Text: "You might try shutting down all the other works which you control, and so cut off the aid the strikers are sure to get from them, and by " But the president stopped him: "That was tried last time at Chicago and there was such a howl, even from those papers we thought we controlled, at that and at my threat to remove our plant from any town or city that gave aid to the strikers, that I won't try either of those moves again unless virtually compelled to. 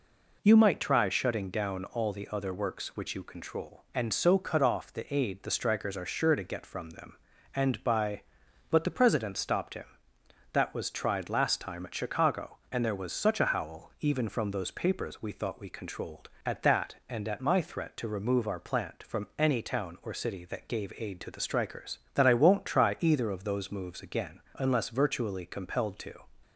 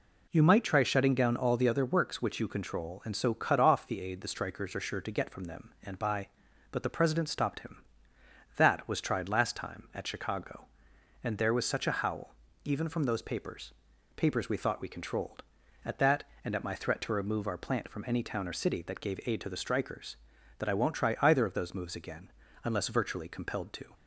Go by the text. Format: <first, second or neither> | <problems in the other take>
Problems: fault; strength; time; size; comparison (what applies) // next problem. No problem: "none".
first | says "papers" twice; at 14.1 s // pauses between "again" and "unless"; slight; at 22.3 s; 0.34 s long; slight in the first